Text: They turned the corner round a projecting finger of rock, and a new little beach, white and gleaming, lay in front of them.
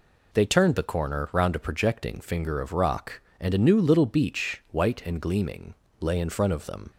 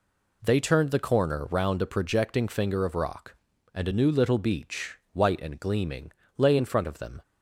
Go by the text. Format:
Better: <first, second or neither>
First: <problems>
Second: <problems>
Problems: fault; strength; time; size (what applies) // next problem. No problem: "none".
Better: neither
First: none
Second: none